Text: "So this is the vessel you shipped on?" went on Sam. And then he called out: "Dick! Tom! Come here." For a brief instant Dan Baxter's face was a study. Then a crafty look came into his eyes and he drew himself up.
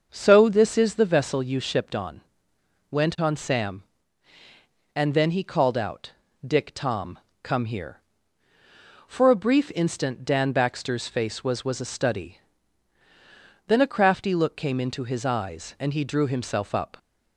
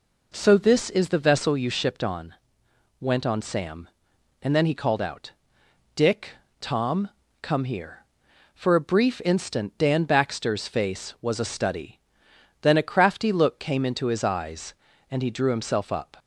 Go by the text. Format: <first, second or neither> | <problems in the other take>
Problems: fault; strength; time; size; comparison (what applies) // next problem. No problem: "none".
second | starts louder than the rest; noticeable; until 1.1 s; 6 dB // says "was" twice; at 11.6 s